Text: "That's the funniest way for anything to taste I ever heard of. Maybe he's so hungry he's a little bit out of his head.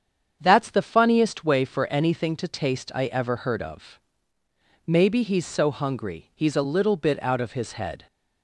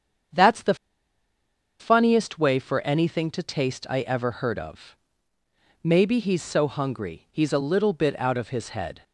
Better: first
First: starts louder than the rest; strong; until 1.4 s; 7.5 dB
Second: starts louder than the rest; strong; until 2.3 s; 7.5 dB // pauses between "the" and "funniest"; at 0.7 s; 1.0 s long

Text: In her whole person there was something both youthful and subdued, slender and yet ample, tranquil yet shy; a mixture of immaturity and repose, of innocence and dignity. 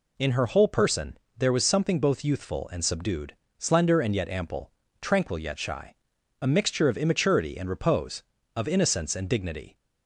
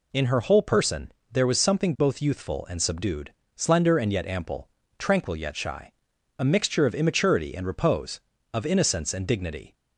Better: neither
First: pauses between "person" and "there"; slight; at 1.1 s; 0.18 s long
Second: pauses between "person" and "there"; slight; at 1.1 s; 0.18 s long

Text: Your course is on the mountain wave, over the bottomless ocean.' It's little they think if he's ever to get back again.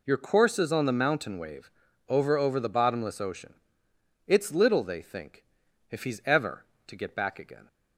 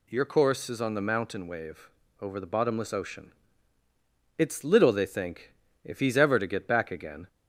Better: second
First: says "over" twice; at 2.3 s // pauses between "think" and "if"; noticeable; at 5.4 s; 0.46 s long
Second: pauses between "think" and "if"; slight; at 5.5 s; 0.32 s long

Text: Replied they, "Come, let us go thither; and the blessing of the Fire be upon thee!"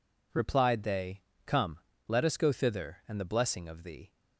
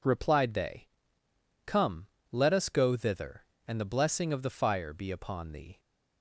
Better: second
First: skips "the Fire be upon"; at 3.8 s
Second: none

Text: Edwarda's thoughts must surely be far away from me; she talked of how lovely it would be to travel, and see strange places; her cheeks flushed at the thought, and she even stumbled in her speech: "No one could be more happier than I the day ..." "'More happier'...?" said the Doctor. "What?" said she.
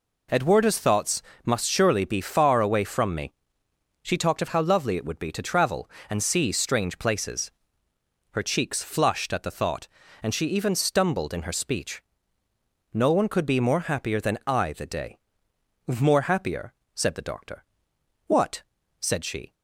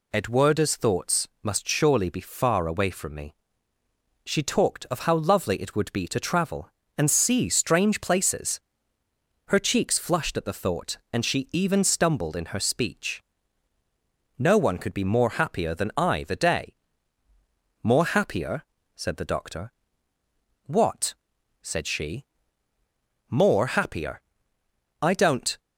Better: first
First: pauses between "thoughts" and "must"; slight; at 1.2 s; 0.22 s long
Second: pauses between "thoughts" and "must"; slight; at 1.2 s; 0.16 s long // goes on to say "More happier I don't"; strong; from 23.3 s on; 2.2 s long

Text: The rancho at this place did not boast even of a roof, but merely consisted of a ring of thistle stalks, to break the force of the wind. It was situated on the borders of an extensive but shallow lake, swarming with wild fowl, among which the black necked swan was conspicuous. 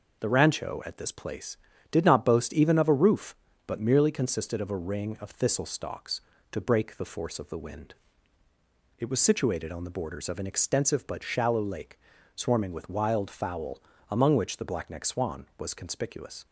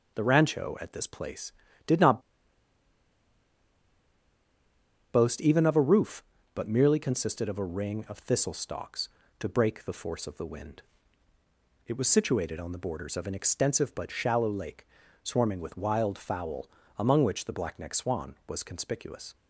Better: first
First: none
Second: pauses between "not" and "boast"; strong; at 2.1 s; 2.9 s long

